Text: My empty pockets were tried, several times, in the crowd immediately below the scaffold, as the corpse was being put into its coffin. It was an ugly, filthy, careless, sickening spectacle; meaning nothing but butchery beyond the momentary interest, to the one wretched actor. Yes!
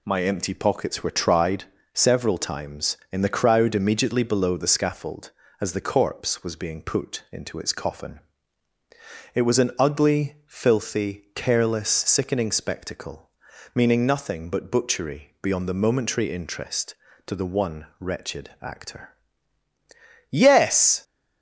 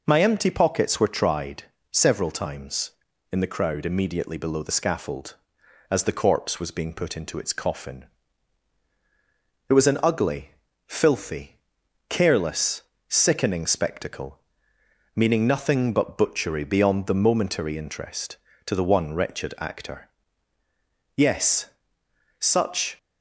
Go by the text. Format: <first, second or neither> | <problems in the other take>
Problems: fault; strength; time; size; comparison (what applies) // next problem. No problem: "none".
first | goes on to say "Such"; from 22.3 s on; 0.58 s long